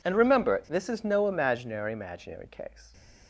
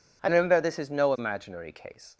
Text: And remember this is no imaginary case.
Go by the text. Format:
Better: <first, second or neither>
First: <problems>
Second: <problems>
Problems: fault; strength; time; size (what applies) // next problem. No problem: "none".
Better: second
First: says "imaginary" twice; at 1.9 s // stays silent after the last word; slight; from 2.6 s on; 0.6 s long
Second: none